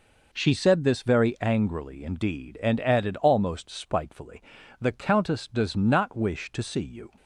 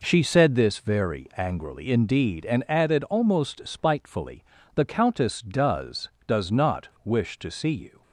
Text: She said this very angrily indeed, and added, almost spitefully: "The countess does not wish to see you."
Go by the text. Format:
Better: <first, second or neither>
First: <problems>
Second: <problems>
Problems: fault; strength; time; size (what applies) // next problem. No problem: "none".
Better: first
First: none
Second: says "does" twice; at 6.2 s // pauses between "not" and "wish"; slight; at 6.8 s; 0.15 s long